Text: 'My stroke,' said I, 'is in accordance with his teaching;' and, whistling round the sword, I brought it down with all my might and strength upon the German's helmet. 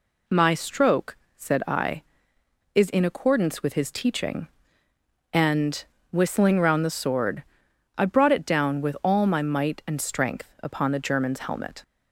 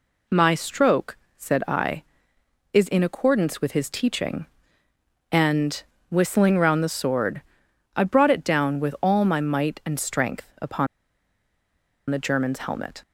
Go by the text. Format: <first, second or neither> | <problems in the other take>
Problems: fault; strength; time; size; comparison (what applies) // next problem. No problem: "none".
first | pauses between "upon" and "the"; at 10.8 s; 1.2 s long